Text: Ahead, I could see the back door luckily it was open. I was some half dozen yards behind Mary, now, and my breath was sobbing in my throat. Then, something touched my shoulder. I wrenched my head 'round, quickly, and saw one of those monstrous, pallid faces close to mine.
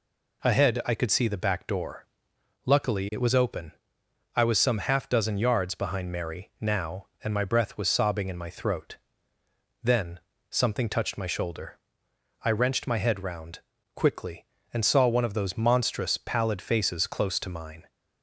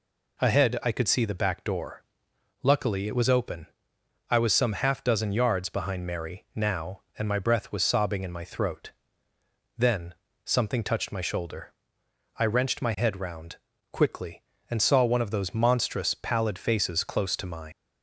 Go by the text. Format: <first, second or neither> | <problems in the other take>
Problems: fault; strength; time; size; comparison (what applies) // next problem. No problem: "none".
first | pauses between "door" and "luckily"; noticeable; at 2.0 s; 0.60 s long; noticeable in the first // leaves "mine" unfinished; at 17.7 s; 130 ms